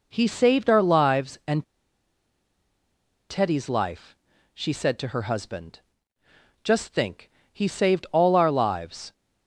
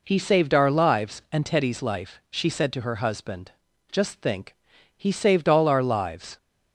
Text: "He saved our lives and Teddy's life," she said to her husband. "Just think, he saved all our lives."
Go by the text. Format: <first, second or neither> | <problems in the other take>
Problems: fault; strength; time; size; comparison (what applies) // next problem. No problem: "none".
second | pauses between "and" and "Teddy's"; strong; at 1.6 s; 1.6 s long